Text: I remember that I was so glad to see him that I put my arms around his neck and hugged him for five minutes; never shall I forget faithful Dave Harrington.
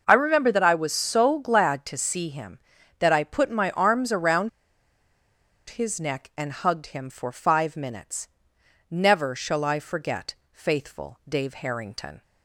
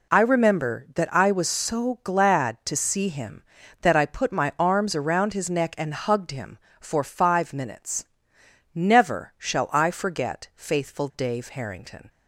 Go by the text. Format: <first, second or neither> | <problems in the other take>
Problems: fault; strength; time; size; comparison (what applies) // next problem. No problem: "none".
second | pauses between "around" and "his"; at 4.4 s; 1.2 s long // pauses between "forget" and "faithful"; slight; at 10.3 s; 0.18 s long